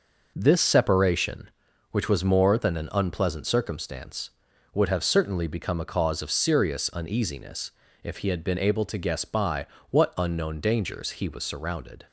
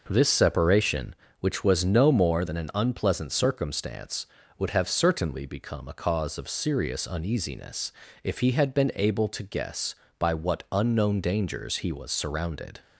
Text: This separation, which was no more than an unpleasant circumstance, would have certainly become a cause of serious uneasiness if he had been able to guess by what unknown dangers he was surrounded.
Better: second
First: skips "no"; at 2.2 s // pauses between "uneasiness" and "if"; slight; at 7.6 s; 0.32 s long // pauses between "by" and "what"; slight; at 9.6 s; 0.24 s long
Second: pauses between "uneasiness" and "if"; slight; at 7.9 s; 0.32 s long

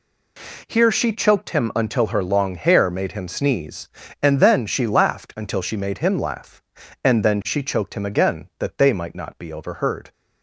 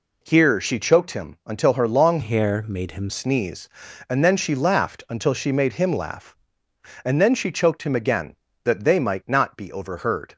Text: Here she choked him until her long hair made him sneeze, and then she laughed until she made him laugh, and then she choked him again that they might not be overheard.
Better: first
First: none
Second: changes voice from "hair" to "him"; from 2.2 to 3.1 s; 0.9 s long

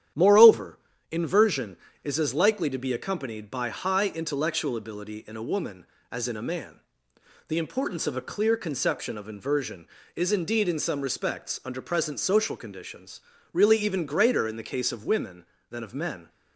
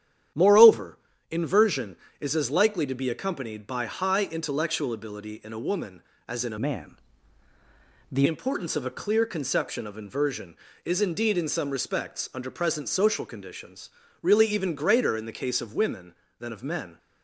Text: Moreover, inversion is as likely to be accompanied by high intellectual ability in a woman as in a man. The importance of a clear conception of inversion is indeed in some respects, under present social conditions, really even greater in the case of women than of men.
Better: first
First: starts louder than the rest; strong; until 1.4 s; 10 dB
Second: starts louder than the rest; strong; until 1.6 s; 10 dB // changes voice from "man" to "The"; from 6.6 to 8.2 s; 1.6 s long

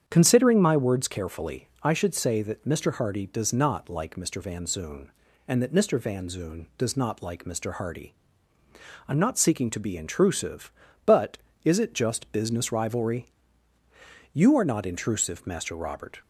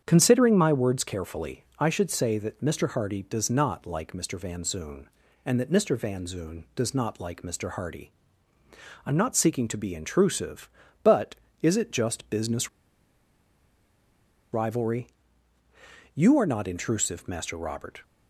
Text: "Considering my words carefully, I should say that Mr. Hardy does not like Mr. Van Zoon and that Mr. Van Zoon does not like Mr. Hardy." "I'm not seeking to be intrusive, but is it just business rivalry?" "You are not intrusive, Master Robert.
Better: first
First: starts louder than the rest; strong; until 1.0 s; 8 dB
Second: starts louder than the rest; strong; until 1.0 s; 8 dB // pauses between "business" and "rivalry"; strong; at 12.6 s; 1.8 s long

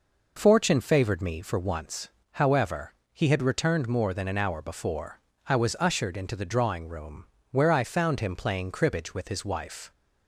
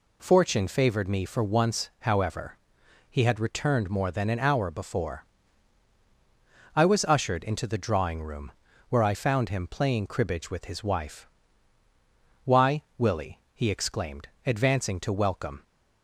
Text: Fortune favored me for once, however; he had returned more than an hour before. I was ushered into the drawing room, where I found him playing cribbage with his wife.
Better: first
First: none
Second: goes on to say "Why Willie he exclaimed advancing to welcome"; strong; from 12.4 s on; 3.1 s long

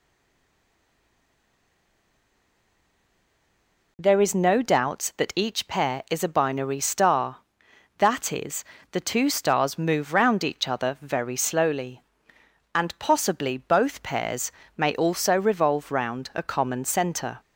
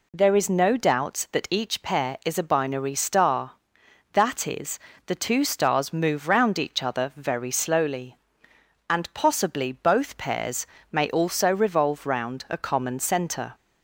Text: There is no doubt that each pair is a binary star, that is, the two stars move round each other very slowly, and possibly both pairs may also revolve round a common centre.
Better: second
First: stays silent before the first word; strong; until 3.9 s; 3.9 s long // pauses between "pairs" and "may"; slight; at 14.4 s; 0.26 s long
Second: pauses between "pairs" and "may"; slight; at 10.6 s; 0.26 s long

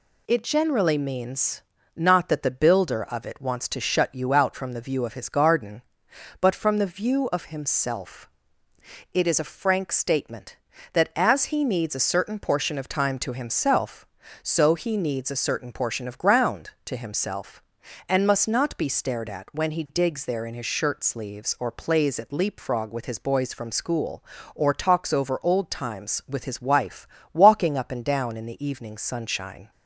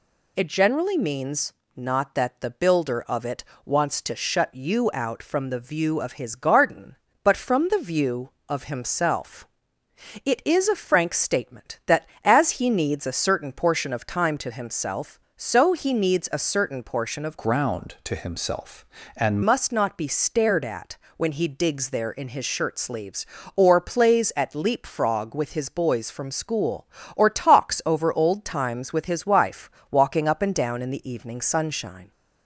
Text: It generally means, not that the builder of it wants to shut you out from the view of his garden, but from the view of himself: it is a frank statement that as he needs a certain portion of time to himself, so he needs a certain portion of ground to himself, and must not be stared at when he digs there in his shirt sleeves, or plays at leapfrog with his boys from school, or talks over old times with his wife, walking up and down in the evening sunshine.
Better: first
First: none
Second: pauses between "it" and "wants"; slight; at 3.4 s; 0.20 s long // changes voice from "ground" to "and"; from 17.3 to 19.4 s; 2.1 s long // pauses between "at" and "when"; slight; at 20.9 s; 0.20 s long

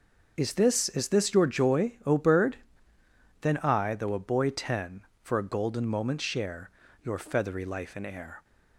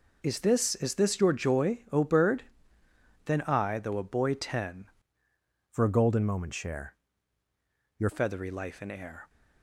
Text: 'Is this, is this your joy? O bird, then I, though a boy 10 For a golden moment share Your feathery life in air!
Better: first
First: pauses between "share" and "Your"; slight; at 6.6 s; 0.34 s long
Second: changes voice from "For" to "Your"; from 5.7 to 8.0 s; 2.3 s long // pauses between "share" and "Your"; at 6.9 s; 1.0 s long

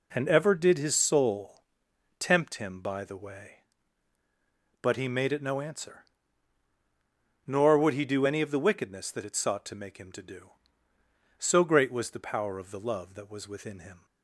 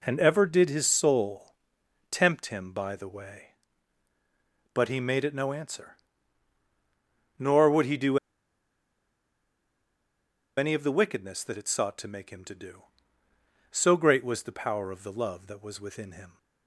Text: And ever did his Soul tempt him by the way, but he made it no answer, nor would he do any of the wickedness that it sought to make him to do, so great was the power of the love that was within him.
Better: first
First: pauses between "Soul" and "tempt"; noticeable; at 1.6 s; 0.56 s long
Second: pauses between "Soul" and "tempt"; noticeable; at 1.5 s; 0.56 s long // pauses between "do" and "any"; strong; at 8.1 s; 2.3 s long

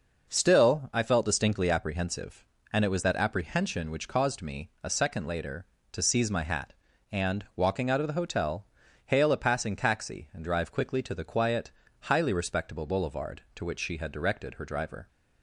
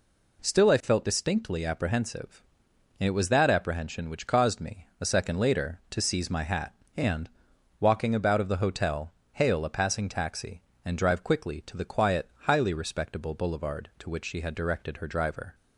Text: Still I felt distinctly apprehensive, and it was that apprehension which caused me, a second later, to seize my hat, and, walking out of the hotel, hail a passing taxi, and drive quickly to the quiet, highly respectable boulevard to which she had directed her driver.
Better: first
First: none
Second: says "about" for "out"; at 8.1 s

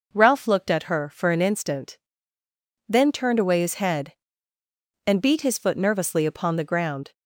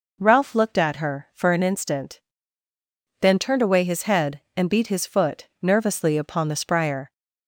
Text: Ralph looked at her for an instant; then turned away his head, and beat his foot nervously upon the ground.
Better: first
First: none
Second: pauses between "foot" and "nervously"; slight; at 5.4 s; 0.16 s long // says "spryer" for "ground"; at 6.5 s

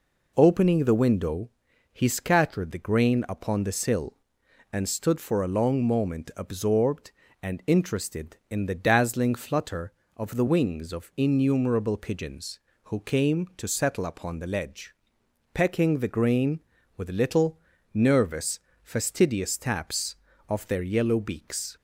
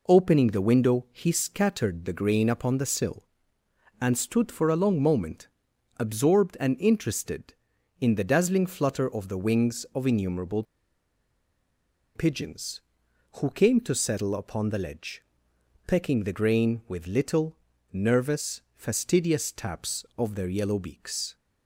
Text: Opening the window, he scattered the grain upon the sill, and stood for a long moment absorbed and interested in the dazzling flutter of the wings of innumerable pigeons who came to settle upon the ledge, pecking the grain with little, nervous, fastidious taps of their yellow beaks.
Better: first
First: none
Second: pauses between "moment" and "absorbed"; noticeable; at 5.4 s; 0.52 s long // pauses between "innumerable" and "pigeons"; strong; at 10.6 s; 1.5 s long

